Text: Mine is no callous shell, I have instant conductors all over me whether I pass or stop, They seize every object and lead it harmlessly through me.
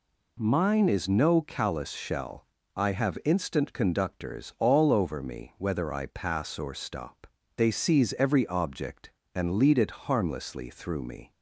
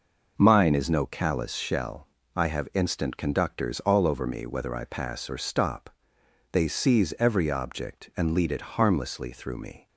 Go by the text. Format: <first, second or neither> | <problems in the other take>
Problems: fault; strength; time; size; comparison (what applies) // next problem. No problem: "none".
neither | none